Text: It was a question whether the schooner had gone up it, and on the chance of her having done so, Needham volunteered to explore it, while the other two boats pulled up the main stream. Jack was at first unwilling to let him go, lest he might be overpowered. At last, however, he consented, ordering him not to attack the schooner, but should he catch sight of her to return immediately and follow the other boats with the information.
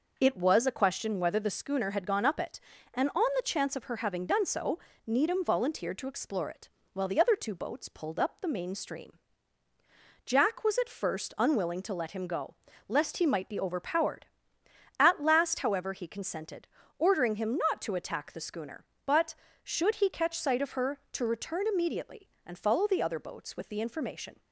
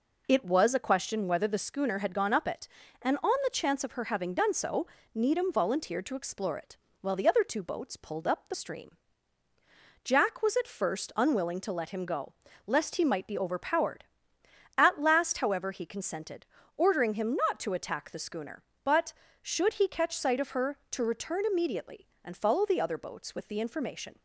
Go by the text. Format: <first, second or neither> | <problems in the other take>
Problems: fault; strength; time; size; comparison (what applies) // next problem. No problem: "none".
first | skips "main"; at 8.5 s